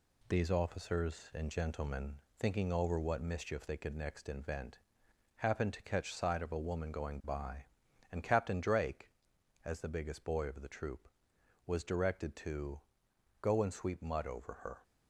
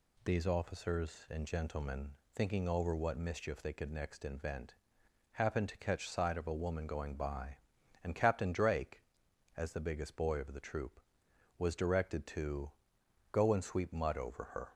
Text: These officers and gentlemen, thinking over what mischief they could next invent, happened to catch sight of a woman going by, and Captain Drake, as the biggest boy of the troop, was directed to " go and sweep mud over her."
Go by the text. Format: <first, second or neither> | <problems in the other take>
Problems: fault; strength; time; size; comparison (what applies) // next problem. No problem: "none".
second | gets quieter; strong; throughout; 7 dB